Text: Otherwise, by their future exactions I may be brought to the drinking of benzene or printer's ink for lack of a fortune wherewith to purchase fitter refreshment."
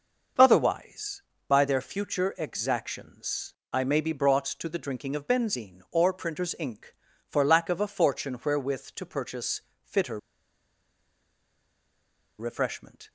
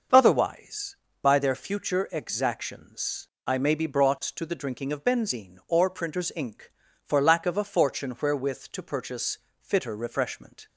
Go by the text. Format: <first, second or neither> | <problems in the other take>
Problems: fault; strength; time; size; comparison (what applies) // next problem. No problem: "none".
second | starts louder than the rest; noticeable; until 1.6 s; 6 dB; noticeable in the second // pauses between "exactions" and "I"; slight; at 3.5 s; 0.18 s long; slight in the second // pauses between "purchase" and "fitter"; slight; at 9.6 s; 0.26 s long; slight in the second // pauses between "fitter" and "refreshment"; strong; at 10.1 s; 2.1 s long